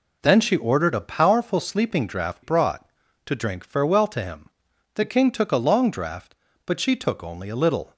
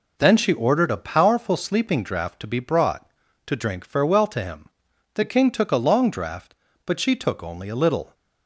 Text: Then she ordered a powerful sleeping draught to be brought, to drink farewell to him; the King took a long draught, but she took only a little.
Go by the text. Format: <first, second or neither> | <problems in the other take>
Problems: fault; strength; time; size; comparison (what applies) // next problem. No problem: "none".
second | skips "to be"; at 2.4 s